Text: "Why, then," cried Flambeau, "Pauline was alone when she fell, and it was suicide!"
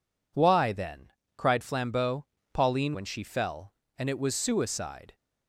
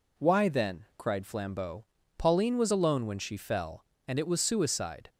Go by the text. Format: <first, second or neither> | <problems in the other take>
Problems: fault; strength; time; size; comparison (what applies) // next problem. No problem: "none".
second | skips "was alone"; at 2.9 s